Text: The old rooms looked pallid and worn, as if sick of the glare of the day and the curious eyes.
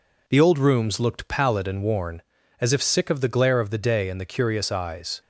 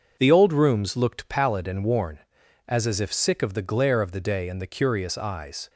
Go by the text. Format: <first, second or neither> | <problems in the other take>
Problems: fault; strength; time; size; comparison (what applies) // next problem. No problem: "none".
first | starts louder than the rest; until 1.2 s; 6.5 dB // says "as" twice; at 2.8 s